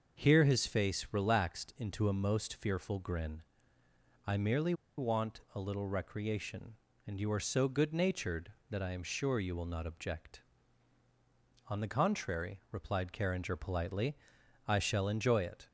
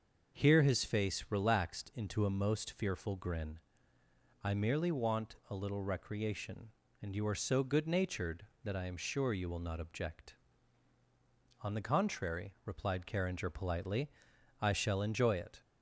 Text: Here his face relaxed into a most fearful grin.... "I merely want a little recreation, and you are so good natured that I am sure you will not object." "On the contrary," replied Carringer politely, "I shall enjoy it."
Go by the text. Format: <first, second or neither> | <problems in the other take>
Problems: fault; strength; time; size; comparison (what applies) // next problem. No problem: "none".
second | starts louder than the rest; until 1.2 s; 6 dB; also in the second // pauses between "merely" and "want"; slight; at 4.7 s; 0.24 s long